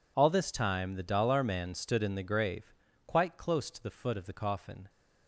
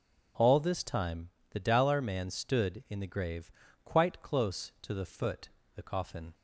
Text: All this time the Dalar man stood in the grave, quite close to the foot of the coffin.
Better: first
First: none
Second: pauses between "time" and "the"; slight; at 1.2 s; 0.22 s long // skips "of"; at 5.6 s

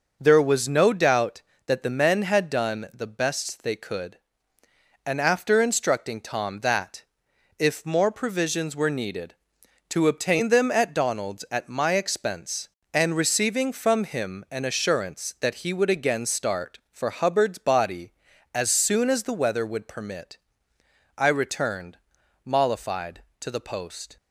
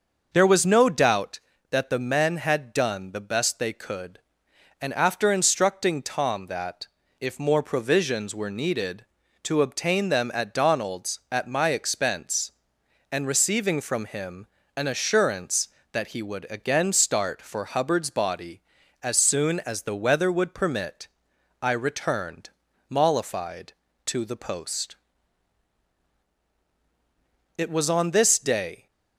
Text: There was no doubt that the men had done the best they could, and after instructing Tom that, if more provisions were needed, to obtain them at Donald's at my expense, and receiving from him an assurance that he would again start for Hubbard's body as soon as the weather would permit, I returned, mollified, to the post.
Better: first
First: none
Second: starts louder than the rest; noticeable; until 1.3 s; 6 dB // pauses between "him" and "an"; slight; at 14.4 s; 0.32 s long // goes on to say "It was on this day"; from 27.5 s on; 1.3 s long

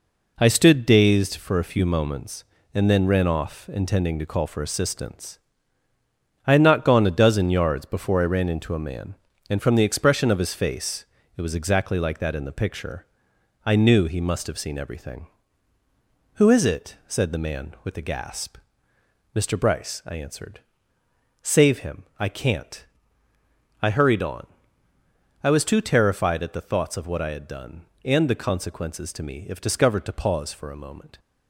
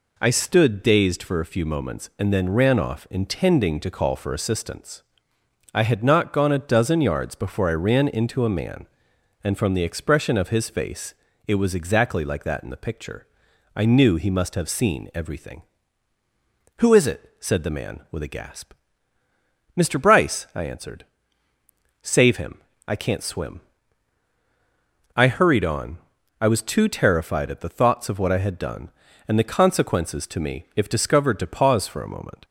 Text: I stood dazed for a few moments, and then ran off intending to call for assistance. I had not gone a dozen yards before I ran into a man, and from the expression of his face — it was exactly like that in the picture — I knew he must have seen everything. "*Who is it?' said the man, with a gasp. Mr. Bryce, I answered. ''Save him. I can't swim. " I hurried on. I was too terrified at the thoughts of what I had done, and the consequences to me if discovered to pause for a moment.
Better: second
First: skips "swim"; at 23.0 s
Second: none

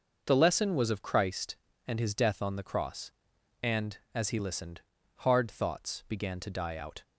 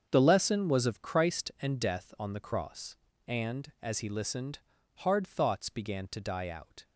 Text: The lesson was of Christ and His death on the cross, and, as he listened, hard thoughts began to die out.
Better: first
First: none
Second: starts louder than the rest; until 1.1 s; 7 dB // skips "His"; at 1.7 s

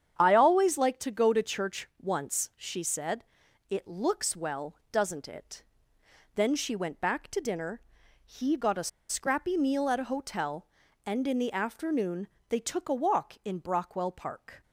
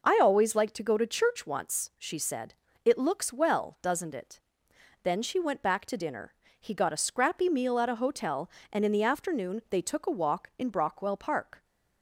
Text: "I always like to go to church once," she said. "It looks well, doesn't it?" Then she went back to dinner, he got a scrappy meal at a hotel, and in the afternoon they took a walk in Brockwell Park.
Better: second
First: starts louder than the rest; strong; until 1.2 s; 8.5 dB // pauses between "a" and "scrappy"; slight; at 8.8 s; 0.20 s long // pauses between "afternoon" and "they"; slight; at 12.2 s; 0.24 s long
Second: none

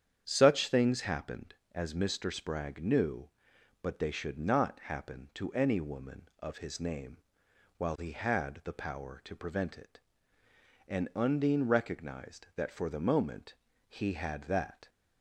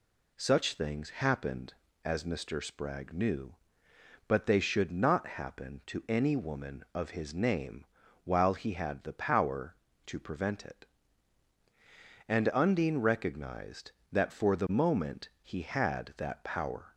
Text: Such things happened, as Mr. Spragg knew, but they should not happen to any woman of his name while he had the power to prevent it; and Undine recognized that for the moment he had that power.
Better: second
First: starts louder than the rest; strong; until 1.2 s; 8.5 dB // pauses between "name" and "while"; noticeable; at 7.1 s; 0.58 s long // pauses between "moment" and "he"; slight; at 13.5 s; 0.32 s long // stops before "power"; at 14.8 s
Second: pauses between "name" and "while"; at 7.8 s; 0.38 s long

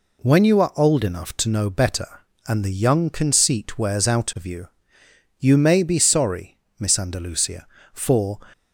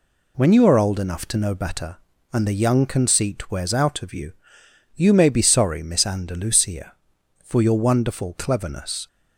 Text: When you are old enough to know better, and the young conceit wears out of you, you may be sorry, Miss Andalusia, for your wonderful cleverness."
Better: second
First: stops before "your wonderful cleverness"; at 8.5 s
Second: none

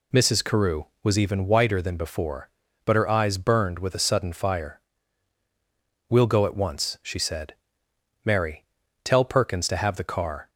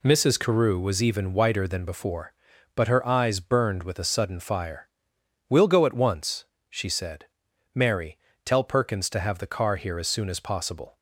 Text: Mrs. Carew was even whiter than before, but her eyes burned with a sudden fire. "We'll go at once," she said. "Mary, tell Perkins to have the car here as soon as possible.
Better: second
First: stops before "here as soon as possible"; at 10.4 s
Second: none

